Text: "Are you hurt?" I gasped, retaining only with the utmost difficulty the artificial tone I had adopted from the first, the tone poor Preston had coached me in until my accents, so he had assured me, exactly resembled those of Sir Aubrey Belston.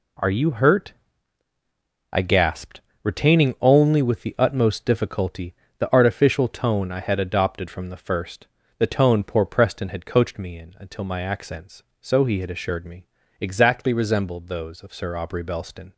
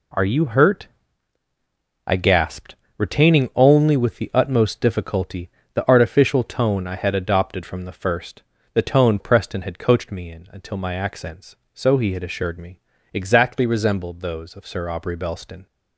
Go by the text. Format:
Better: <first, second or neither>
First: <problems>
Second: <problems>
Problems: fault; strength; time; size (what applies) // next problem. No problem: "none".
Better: first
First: pauses between "difficulty" and "the"; slight; at 5.5 s; 0.24 s long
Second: pauses between "difficulty" and "the"; slight; at 5.4 s; 0.24 s long // skips "poor"; at 9.1 s